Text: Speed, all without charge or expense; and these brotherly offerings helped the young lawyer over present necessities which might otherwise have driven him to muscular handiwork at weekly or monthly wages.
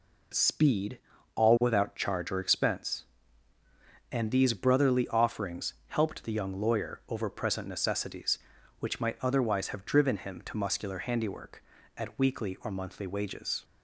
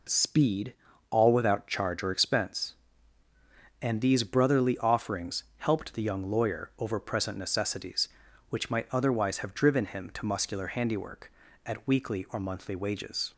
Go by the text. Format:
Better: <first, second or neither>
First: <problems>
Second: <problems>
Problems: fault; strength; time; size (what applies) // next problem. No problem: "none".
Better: neither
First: pauses between "offerings" and "helped"; slight; at 5.7 s; 0.16 s long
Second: pauses between "offerings" and "helped"; slight; at 5.4 s; 0.16 s long